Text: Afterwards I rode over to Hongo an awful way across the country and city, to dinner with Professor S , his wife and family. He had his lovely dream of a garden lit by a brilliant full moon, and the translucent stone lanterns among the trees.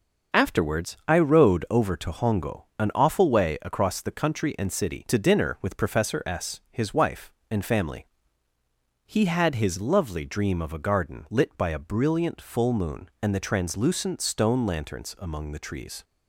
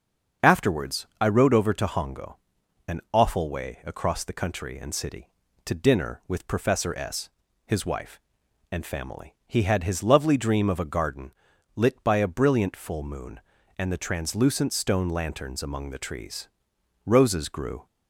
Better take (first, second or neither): first